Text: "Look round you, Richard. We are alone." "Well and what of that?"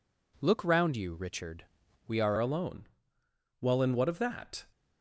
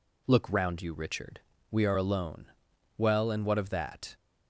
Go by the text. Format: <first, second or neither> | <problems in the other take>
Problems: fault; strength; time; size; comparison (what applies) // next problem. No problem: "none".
second | changes voice at "alone"; from 2.3 s on; 2.3 s long